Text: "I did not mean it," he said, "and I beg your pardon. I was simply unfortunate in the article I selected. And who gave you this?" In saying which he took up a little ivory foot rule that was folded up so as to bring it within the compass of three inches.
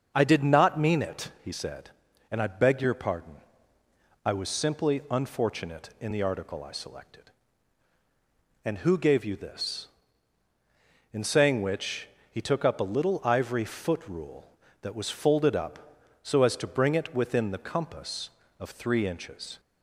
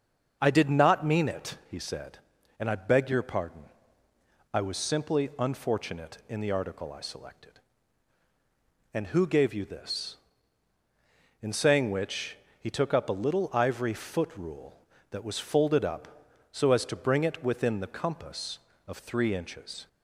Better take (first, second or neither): neither